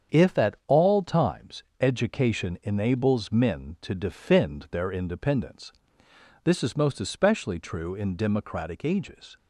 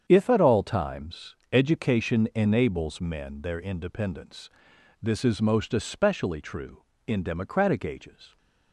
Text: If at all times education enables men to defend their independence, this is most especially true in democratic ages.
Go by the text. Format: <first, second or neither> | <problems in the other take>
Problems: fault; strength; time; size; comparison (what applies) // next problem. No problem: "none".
first | starts louder than the rest; strong; until 1.0 s; 8 dB; strong in the first // pauses between "times" and "education"; slight; at 1.3 s; 0.16 s long; slight in the first // skips "to defend"; at 3.4 s